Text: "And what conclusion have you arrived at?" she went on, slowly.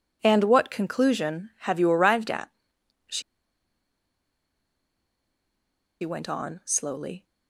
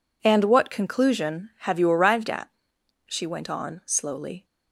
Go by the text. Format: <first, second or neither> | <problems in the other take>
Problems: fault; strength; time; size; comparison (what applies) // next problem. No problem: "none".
second | pauses between "she" and "went"; strong; at 3.2 s; 2.8 s long